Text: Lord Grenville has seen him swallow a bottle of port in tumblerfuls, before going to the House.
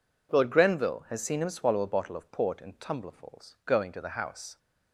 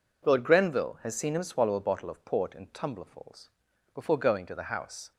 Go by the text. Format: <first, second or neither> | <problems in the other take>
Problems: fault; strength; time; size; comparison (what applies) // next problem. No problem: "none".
second | skips "before"; at 3.6 s